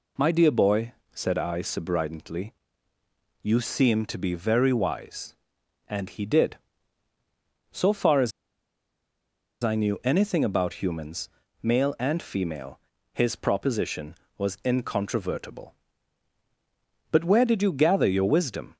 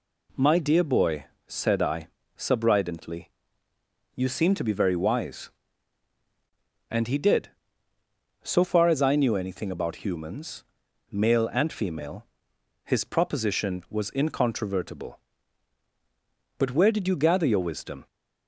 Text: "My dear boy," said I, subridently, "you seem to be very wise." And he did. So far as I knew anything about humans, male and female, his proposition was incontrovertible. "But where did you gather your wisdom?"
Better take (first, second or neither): second